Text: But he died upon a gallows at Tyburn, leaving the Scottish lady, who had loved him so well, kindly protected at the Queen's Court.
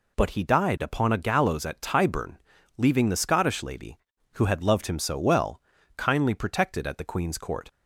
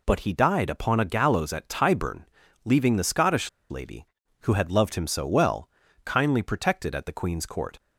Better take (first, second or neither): first